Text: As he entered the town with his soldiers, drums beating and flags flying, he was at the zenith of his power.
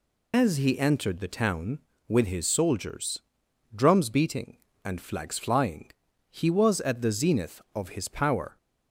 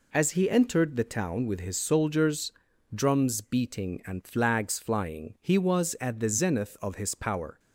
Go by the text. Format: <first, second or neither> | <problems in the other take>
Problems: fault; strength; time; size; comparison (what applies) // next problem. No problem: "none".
second | loses the start of "As"; at 0.3 s; 80 ms